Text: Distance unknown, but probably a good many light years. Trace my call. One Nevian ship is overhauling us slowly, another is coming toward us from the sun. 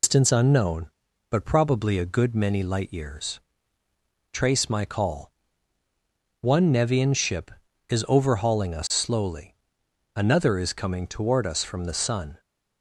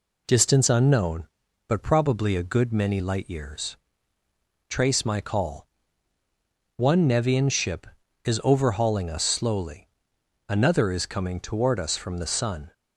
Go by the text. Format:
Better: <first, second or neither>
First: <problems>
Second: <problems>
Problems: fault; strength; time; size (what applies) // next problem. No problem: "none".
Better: second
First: loses the start of "Distance"; at 0.0 s; 140 ms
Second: none